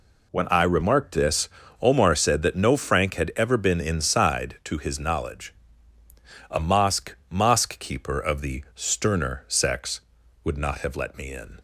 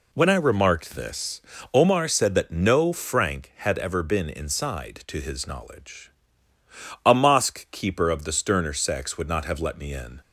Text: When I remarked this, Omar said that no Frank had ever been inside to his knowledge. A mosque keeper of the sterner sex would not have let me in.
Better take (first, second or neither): second